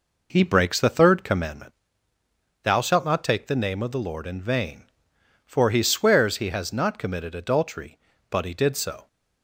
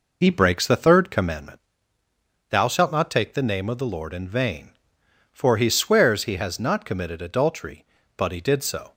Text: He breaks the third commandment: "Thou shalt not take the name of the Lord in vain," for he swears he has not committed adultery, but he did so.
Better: first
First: none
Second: loses the start of "He"; at 0.2 s; 40 ms

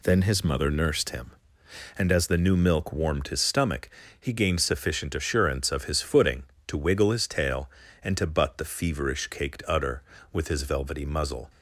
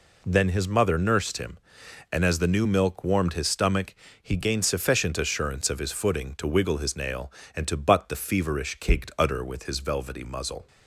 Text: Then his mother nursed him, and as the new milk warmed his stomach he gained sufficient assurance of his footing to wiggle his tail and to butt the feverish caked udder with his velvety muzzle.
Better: first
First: pauses between "stomach" and "he"; slight; at 3.9 s; 0.28 s long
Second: pauses between "stomach" and "he"; slight; at 3.9 s; 0.26 s long // says "nail" for "tail"; at 6.9 s

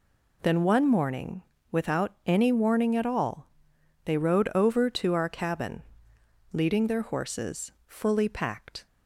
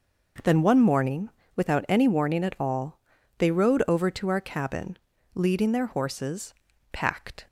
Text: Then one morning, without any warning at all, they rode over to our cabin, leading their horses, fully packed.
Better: first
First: none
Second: skips "fully"; at 6.7 s

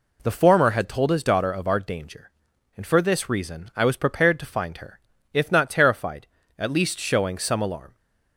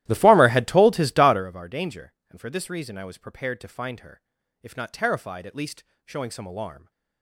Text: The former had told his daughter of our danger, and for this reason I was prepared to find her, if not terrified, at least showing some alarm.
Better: first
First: none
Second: starts louder than the rest; strong; until 1.5 s; 14.5 dB // pauses between "least" and "showing"; slight; at 5.8 s; 0.22 s long

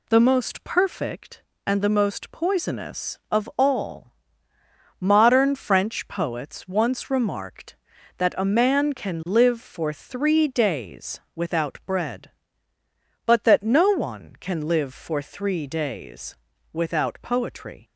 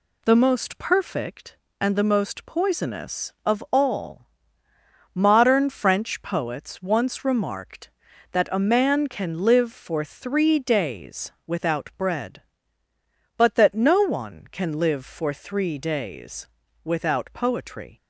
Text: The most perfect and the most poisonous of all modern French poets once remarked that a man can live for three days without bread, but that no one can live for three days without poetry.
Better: neither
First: pauses between "all" and "modern"; noticeable; at 4.1 s; 0.88 s long // pauses between "days" and "without"; slight; at 16.3 s; 0.36 s long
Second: pauses between "all" and "modern"; noticeable; at 4.2 s; 0.88 s long // pauses between "days" and "without"; slight; at 16.4 s; 0.36 s long

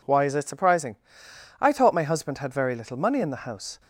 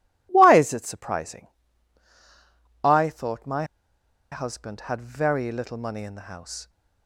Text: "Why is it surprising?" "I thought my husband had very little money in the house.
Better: first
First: none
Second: pauses between "my" and "husband"; noticeable; at 3.6 s; 0.67 s long

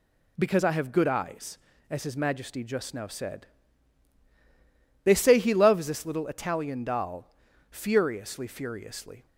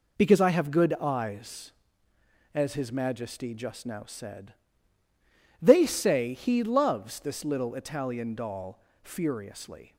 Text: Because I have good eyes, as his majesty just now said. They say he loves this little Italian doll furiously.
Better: second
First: pauses between "doll" and "furiously"; at 7.2 s; 0.42 s long // says "furiously" twice; at 8.4 s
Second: pauses between "doll" and "furiously"; slight; at 8.7 s; 0.24 s long

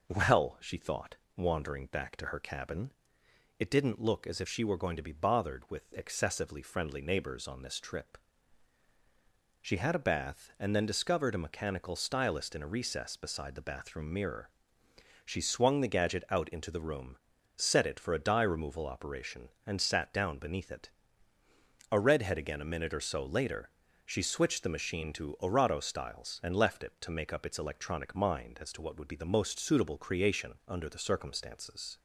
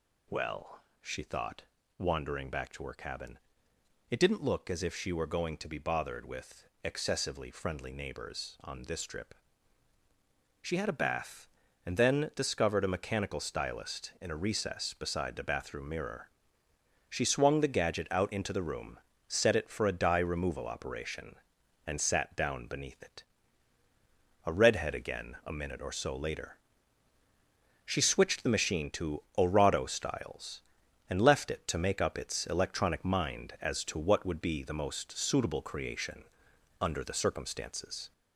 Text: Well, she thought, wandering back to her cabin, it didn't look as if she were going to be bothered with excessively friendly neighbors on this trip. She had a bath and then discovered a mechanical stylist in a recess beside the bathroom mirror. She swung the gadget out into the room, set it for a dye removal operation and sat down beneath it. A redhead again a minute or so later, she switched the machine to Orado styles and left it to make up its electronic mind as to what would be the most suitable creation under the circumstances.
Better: first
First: none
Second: gets louder; slight; throughout; 3.5 dB // pauses between "with" and "excessively"; slight; at 6.6 s; 0.18 s long // pauses between "creation" and "under"; noticeable; at 36.2 s; 0.58 s long

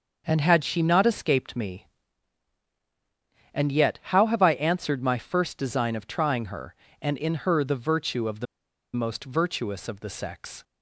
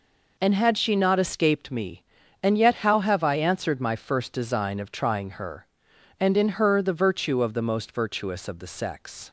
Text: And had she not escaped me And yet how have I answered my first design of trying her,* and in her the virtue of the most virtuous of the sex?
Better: second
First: starts louder than the rest; until 1.2 s; 6.5 dB // pauses between "the" and "most"; noticeable; at 8.4 s; 0.49 s long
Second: none

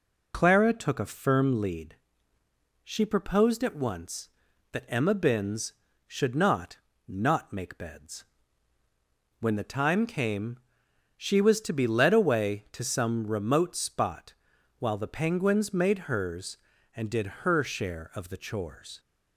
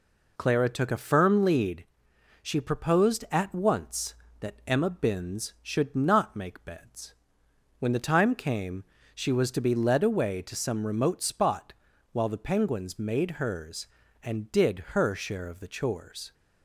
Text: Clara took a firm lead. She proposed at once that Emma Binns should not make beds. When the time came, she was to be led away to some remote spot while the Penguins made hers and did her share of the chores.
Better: second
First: says "not" twice; at 7.0 s // pauses between "spot" and "while"; at 14.3 s; 0.44 s long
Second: pauses between "spot" and "while"; at 11.7 s; 0.40 s long

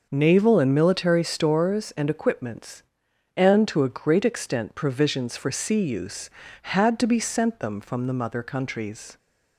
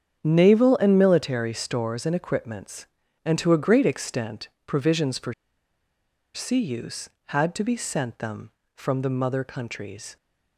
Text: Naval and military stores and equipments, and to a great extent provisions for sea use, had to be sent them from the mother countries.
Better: first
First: none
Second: starts louder than the rest; strong; until 1.2 s; 8 dB // pauses between "extent" and "provisions"; slight; at 4.4 s; 0.16 s long // pauses between "for" and "sea"; at 5.3 s; 1.0 s long

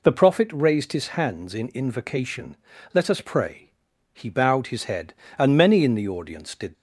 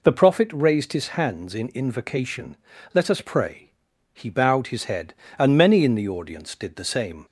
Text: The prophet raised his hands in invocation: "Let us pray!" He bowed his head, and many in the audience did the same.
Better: second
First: stops before "the same"; at 6.7 s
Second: none

